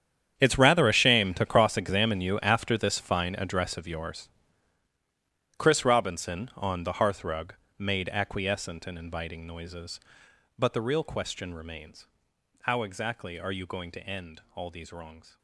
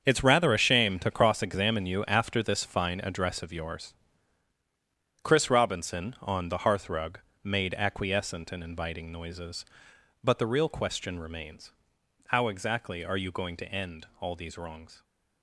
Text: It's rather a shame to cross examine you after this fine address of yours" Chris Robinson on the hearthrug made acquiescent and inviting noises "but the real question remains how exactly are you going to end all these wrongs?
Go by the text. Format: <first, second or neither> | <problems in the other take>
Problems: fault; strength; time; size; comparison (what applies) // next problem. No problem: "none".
second | gets quieter; strong; throughout; 16.5 dB // starts louder than the rest; strong; until 1.4 s; 9 dB; strong in the second // pauses between "yours" and "Chris"; strong; at 4.2 s; 1.2 s long; strong in the second // pauses between "hearthrug" and "made"; slight; at 7.5 s; 0.26 s long; slight in the second // pauses between "remains" and "how"; noticeable; at 12.0 s; 0.58 s long; noticeable in the second